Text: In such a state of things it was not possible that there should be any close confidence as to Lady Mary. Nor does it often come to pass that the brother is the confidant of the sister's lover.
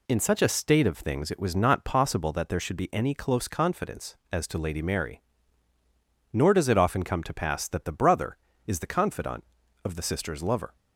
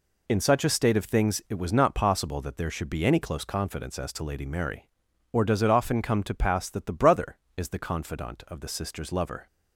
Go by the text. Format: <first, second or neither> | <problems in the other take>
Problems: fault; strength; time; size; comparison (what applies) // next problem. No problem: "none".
first | says "Or" for "Nor"; at 5.3 s